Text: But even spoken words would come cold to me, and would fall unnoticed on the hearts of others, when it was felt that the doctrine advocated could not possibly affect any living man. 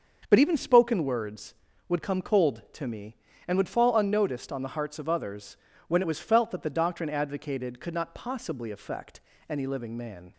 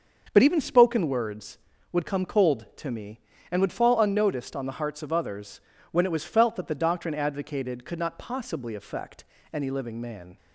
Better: neither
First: starts louder than the rest; until 1.3 s; 6.5 dB // pauses between "affect" and "any"; slight; at 9.2 s; 0.28 s long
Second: starts louder than the rest; until 1.3 s; 6.5 dB // pauses between "affect" and "any"; slight; at 9.2 s; 0.28 s long

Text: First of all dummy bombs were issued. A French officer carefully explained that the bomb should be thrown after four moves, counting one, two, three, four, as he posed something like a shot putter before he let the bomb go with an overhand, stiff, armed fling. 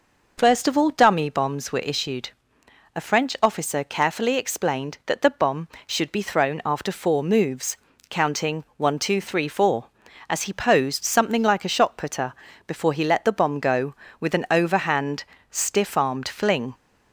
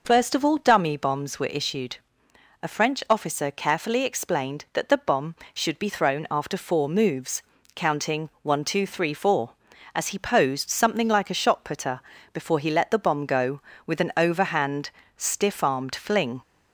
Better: neither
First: pauses between "putter" and "before"; slight; at 12.3 s; 0.34 s long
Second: pauses between "putter" and "before"; slight; at 12.0 s; 0.33 s long

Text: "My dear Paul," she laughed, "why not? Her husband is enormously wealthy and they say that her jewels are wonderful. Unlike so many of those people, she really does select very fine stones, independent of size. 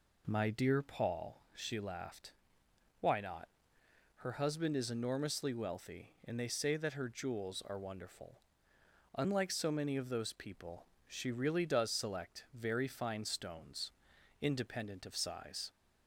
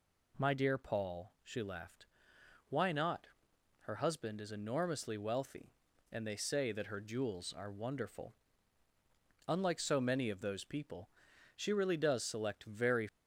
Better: first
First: none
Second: stops before "fine stones independent of size"; at 13.0 s

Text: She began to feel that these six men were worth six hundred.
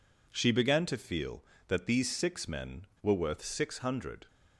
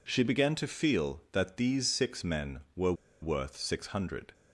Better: first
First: none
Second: pauses between "were" and "worth"; slight; at 2.9 s; 0.28 s long

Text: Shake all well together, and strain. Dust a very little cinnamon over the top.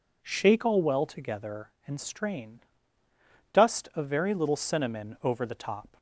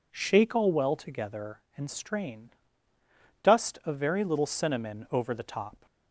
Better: neither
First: none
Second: none

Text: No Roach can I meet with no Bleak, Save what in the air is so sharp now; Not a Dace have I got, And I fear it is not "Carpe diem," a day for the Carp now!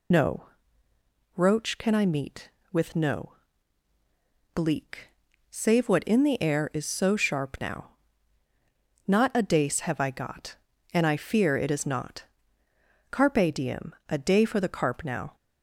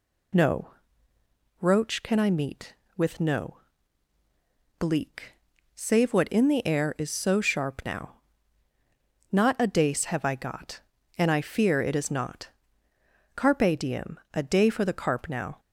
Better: second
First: loses the start of "No"; at 0.1 s; 25 ms // pauses between "No" and "Roach"; noticeable; at 0.4 s; 0.90 s long // pauses between "no" and "Bleak"; at 3.3 s; 1.2 s long // pauses between "not" and "Carpe"; noticeable; at 12.2 s; 0.88 s long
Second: pauses between "No" and "Roach"; noticeable; at 0.7 s; 0.90 s long // pauses between "no" and "Bleak"; at 3.5 s; 1.2 s long // pauses between "not" and "Carpe"; noticeable; at 12.4 s; 0.88 s long

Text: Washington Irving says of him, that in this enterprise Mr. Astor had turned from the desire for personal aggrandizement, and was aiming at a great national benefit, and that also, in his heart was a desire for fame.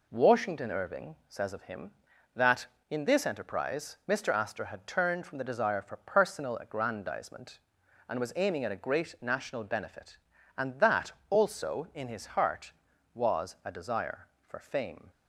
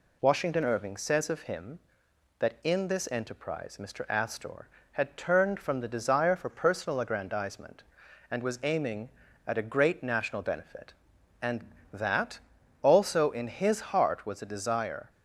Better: first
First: pauses between "that" and "also"; slight; at 11.1 s; 0.18 s long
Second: pauses between "that" and "also"; at 12.3 s; 0.44 s long // stops before "for fame"; at 15.0 s

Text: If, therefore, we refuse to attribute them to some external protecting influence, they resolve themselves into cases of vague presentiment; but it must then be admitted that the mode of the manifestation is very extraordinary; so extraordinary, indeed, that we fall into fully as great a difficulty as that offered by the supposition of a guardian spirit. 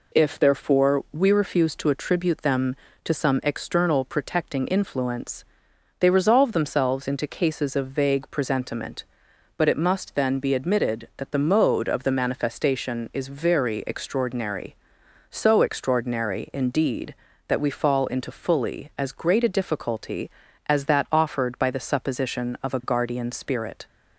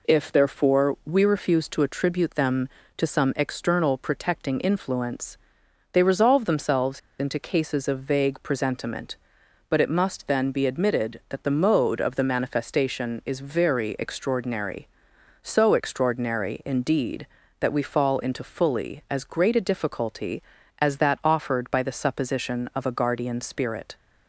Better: first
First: none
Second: pauses between "themselves" and "into"; slight; at 6.9 s; 0.19 s long

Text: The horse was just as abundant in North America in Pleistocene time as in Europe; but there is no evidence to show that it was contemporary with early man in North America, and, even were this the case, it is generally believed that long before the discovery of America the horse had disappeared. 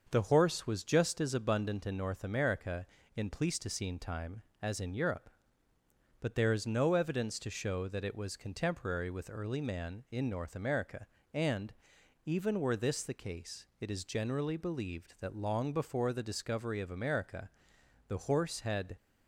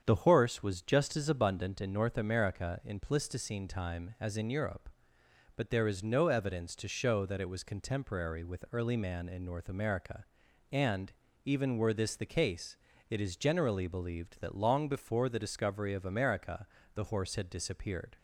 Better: second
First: starts louder than the rest; until 1.1 s; 6.5 dB // pauses between "America" and "the"; noticeable; at 17.4 s; 0.58 s long // stops before "disappeared"; at 18.9 s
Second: starts louder than the rest; strong; until 1.0 s; 7.5 dB // pauses between "America" and "the"; slight; at 16.6 s; 0.28 s long

